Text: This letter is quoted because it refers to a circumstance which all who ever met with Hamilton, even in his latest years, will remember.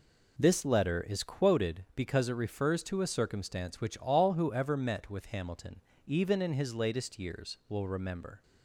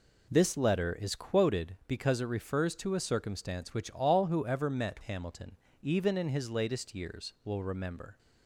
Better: first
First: none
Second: skips "with"; at 5.0 s

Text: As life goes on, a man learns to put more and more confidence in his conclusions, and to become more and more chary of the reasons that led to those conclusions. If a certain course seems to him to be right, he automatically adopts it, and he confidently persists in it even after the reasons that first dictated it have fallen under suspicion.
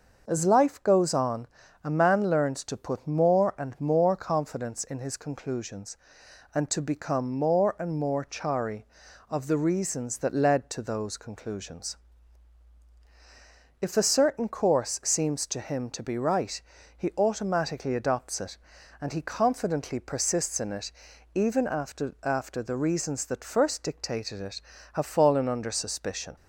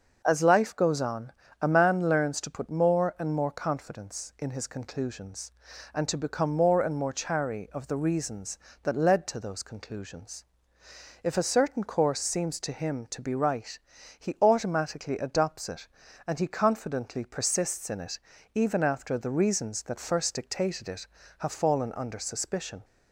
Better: second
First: starts louder than the rest; noticeable; until 1.2 s; 6 dB // pauses between "it" and "even"; noticeable; at 20.8 s; 0.46 s long // says "after" twice; at 22.2 s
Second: starts louder than the rest; noticeable; until 1.2 s; 6 dB // pauses between "it" and "even"; slight; at 18.2 s; 0.34 s long

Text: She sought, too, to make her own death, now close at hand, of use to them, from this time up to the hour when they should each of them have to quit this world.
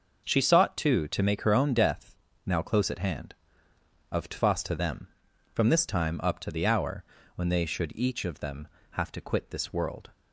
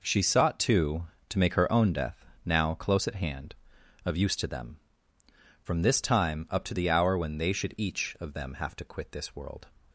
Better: second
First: says "tfas" for "use"; at 4.2 s // pauses between "hour" and "when"; slight; at 7.0 s; 0.30 s long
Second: none

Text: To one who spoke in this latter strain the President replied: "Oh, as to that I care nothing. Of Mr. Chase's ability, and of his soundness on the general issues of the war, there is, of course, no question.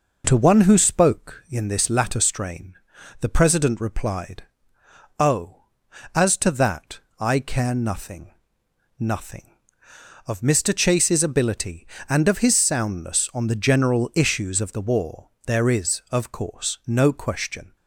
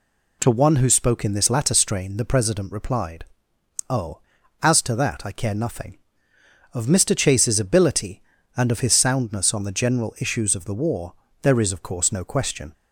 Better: second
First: pauses between "strain" and "the"; noticeable; at 2.7 s; 0.46 s long // pauses between "that" and "I"; slight; at 6.9 s; 0.22 s long // says "nothing" twice; at 8.9 s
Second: none

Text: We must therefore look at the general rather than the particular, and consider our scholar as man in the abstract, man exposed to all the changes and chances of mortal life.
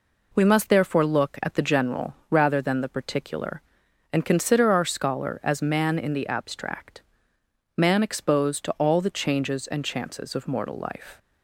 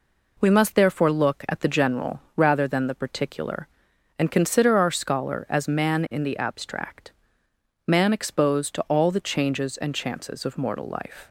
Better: neither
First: pauses between "general" and "rather"; slight; at 2.1 s; 0.16 s long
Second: pauses between "general" and "rather"; slight; at 2.1 s; 0.16 s long

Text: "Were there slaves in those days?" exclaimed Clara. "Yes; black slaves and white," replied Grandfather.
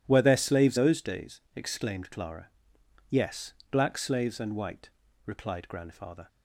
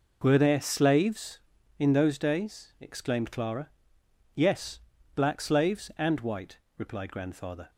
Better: second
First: skips "in"; at 0.7 s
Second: none

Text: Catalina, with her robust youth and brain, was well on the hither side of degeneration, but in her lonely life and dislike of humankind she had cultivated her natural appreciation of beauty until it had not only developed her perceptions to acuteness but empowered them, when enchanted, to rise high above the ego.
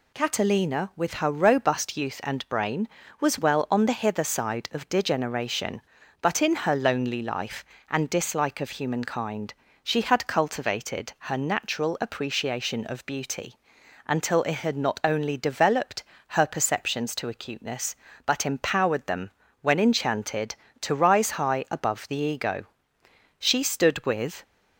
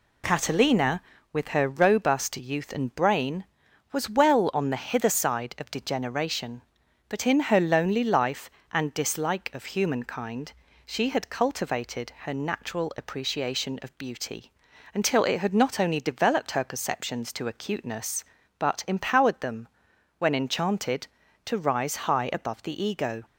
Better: second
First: pauses between "humankind" and "she"; slight; at 9.5 s; 0.30 s long // pauses between "beauty" and "until"; noticeable; at 13.5 s; 0.52 s long // pauses between "developed" and "her"; slight; at 16.0 s; 0.26 s long // goes on to say "She stood with"; noticeable; from 23.3 s on; 1.0 s long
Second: pauses between "humankind" and "she"; slight; at 10.5 s; 0.34 s long // pauses between "beauty" and "until"; at 14.5 s; 0.44 s long

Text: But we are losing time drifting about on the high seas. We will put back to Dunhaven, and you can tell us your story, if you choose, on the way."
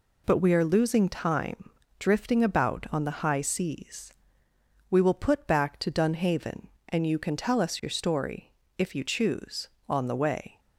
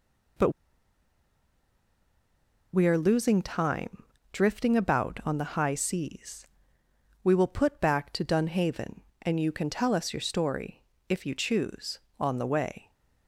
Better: first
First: pauses between "time" and "drifting"; slight; at 1.6 s; 0.30 s long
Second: pauses between "But" and "we"; strong; at 0.4 s; 2.2 s long // pauses between "time" and "drifting"; slight; at 4.0 s; 0.30 s long

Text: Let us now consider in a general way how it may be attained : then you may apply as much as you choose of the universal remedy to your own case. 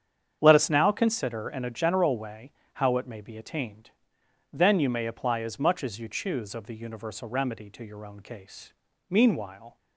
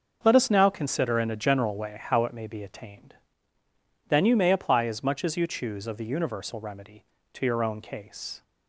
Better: second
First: starts louder than the rest; strong; until 1.4 s; 8.5 dB // pauses between "way" and "how"; slight; at 2.5 s; 0.22 s long // goes on to say "Meanwhile"; noticeable; from 9.0 s on; 0.68 s long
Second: starts louder than the rest; until 1.2 s; 6.5 dB

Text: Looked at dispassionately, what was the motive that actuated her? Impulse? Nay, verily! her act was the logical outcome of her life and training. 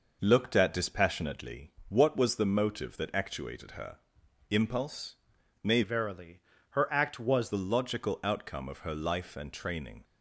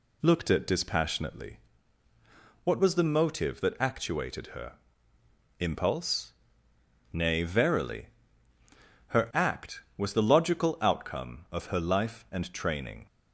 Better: second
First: changes voice from "verily" to "was"; from 5.8 to 7.5 s; 1.7 s long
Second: none

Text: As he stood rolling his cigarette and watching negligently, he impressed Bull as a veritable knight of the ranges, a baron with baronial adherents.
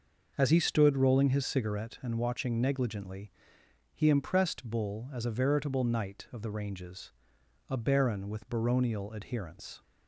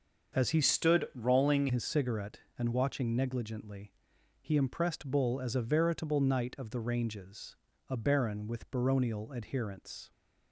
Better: first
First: none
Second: starts louder than the rest; until 1.4 s; 6.5 dB // changes voice from "stood" to "rolling"; from 0.6 to 1.6 s; 1.0 s long

